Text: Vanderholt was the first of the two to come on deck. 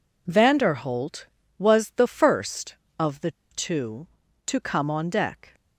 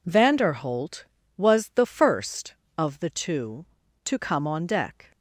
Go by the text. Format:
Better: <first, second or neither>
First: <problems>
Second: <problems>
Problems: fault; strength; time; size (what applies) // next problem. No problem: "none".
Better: second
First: pauses between "the" and "two"; slight; at 3.2 s; 0.22 s long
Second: none